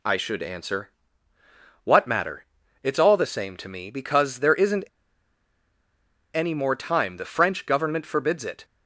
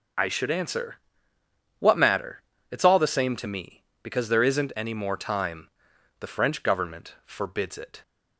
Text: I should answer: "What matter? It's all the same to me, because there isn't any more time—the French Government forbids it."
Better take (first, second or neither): second